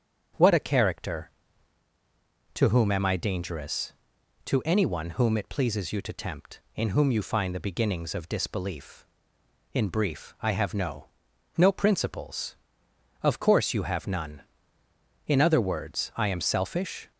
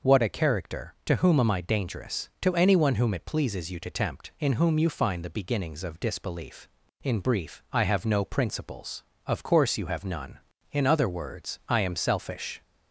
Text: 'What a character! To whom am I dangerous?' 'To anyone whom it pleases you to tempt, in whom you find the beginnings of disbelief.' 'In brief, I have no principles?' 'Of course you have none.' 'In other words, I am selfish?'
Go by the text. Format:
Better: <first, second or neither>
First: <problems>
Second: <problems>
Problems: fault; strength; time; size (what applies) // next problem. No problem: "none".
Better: second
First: starts louder than the rest; strong; until 2.6 s; 7.5 dB // says "no" twice; at 11.5 s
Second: none